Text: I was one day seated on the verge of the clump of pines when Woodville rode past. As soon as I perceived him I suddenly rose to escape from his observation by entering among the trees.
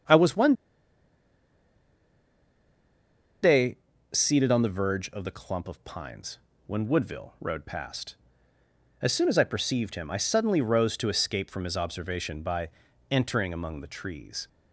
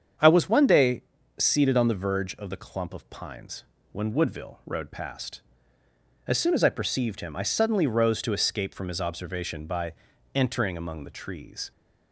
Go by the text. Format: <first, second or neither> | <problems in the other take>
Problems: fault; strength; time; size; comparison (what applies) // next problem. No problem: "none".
second | starts louder than the rest; strong; until 4.3 s; 7.5 dB; strong in the second // pauses between "one" and "day"; strong; at 0.5 s; 2.9 s long // pauses between "day" and "seated"; slight; at 3.7 s; 0.34 s long; slight in the second // pauses between "pines" and "when"; slight; at 6.3 s; 0.28 s long; slight in the second // pauses between "by" and "entering"; at 12.6 s; 0.42 s long; also in the second